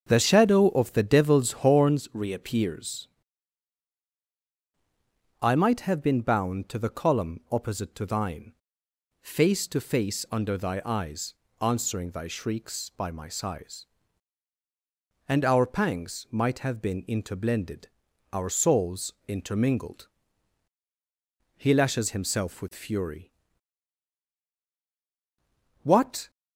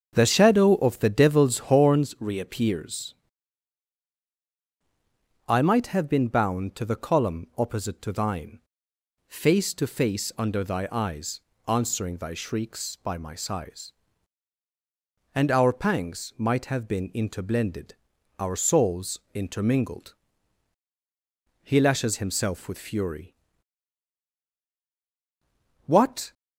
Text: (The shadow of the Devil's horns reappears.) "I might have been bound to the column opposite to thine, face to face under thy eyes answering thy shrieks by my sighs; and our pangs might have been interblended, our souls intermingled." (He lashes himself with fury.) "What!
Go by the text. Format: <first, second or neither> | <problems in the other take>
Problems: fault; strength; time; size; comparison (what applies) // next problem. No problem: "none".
neither | starts louder than the rest; the same in both // pauses between "eyes" and "answering"; slight; the same in both // pauses between "souls" and "intermingled"; slight; the same in both